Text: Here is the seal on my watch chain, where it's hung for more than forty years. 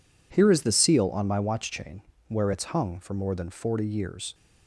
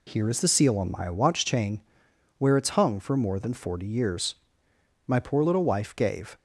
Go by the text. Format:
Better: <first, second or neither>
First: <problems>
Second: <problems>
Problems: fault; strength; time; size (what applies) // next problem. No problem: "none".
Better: first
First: none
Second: goes on to say "My poor little wife gave"; from 5.0 s on; 1.3 s long